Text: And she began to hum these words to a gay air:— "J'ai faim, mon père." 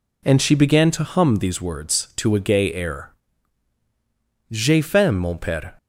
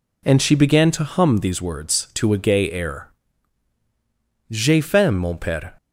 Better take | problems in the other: neither | none

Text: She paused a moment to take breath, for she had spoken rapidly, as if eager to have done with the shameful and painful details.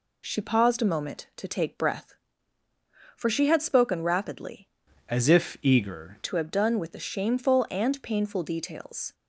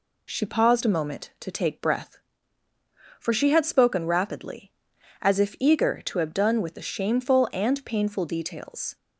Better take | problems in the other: second | changes voice from "as" to "eager"; from 5.0 to 6.1 s; 1.1 s long

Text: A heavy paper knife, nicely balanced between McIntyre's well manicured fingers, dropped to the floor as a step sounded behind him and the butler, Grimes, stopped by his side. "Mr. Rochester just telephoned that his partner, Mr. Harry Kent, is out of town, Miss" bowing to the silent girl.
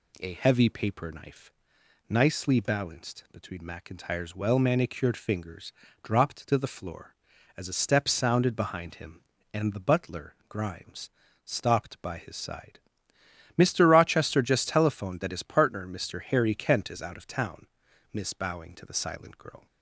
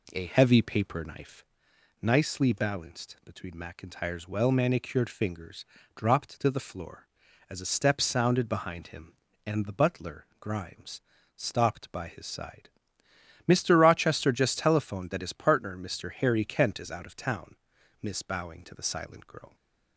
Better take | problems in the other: first | starts louder than the rest; slight; until 1.5 s; 2.5 dB

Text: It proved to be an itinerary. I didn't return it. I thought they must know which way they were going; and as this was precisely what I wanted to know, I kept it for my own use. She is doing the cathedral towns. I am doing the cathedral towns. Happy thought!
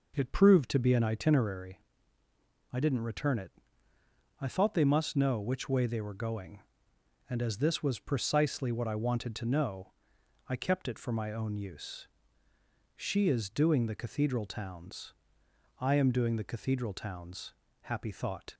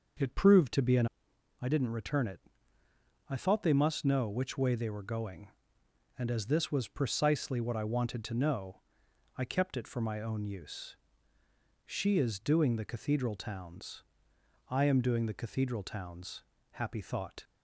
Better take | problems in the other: first | skips "itinerary"; at 1.3 s

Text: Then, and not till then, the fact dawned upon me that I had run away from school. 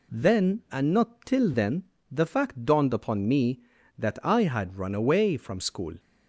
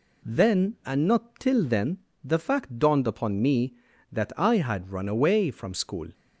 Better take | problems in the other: neither | none

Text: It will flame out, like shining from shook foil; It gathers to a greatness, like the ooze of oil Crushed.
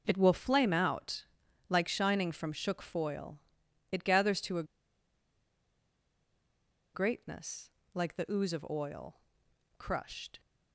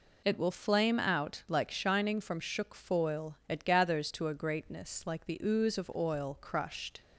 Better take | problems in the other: second | pauses between "a" and "greatness"; strong; at 4.6 s; 2.3 s long // pauses between "oil" and "Crushed"; noticeable; at 9.1 s; 0.58 s long

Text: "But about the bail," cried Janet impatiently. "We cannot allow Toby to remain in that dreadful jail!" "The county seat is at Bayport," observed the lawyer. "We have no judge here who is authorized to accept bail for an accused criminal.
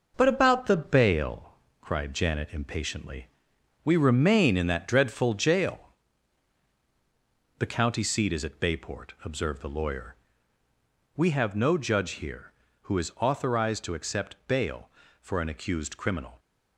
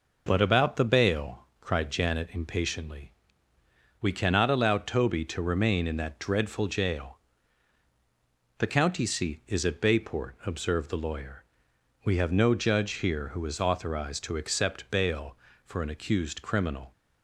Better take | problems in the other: second | skips "cannot allow Toby to"; at 3.9 s

